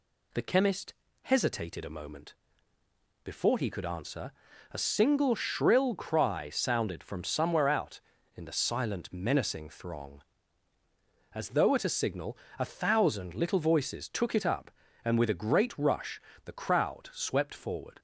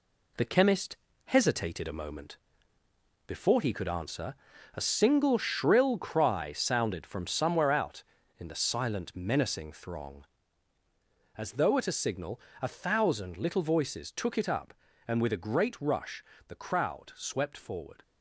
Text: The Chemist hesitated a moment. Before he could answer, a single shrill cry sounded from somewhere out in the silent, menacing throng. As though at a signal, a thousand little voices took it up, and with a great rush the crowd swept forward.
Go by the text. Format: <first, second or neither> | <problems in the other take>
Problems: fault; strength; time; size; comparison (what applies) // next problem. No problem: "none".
first | gets quieter; throughout; 7 dB // pauses between "Chemist" and "hesitated"; slight; at 0.9 s; 0.30 s long; slight in the first // pauses between "rush" and "the"; slight; at 16.2 s; 0.24 s long; slight in the first